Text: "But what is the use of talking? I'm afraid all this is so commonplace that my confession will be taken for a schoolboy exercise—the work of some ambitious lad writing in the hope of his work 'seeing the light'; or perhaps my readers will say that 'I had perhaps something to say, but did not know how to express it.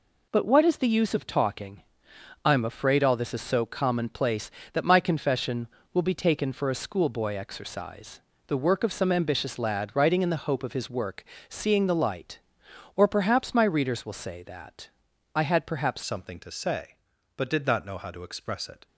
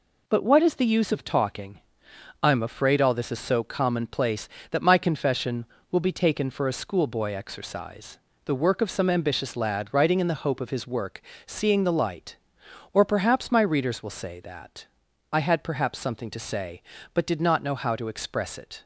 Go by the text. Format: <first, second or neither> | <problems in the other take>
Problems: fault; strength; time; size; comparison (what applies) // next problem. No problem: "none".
second | pauses between "work" and "seeing"; slight; at 11.2 s; 0.24 s long; slight in the second // pauses between "that" and "I"; at 14.8 s; 0.44 s long; also in the second // changes voice at "something"; from 16.0 s on; 2.8 s long